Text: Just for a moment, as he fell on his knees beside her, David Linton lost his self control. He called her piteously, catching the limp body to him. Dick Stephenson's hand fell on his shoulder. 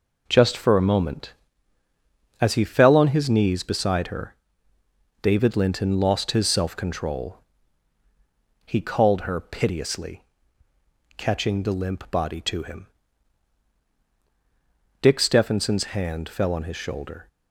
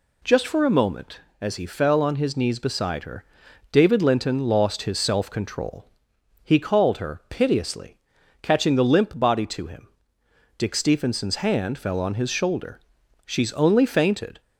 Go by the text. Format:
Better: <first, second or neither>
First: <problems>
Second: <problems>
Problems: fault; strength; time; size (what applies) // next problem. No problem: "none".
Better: first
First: none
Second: goes on to say "She's only fainted"; noticeable; from 13.2 s on; 1.1 s long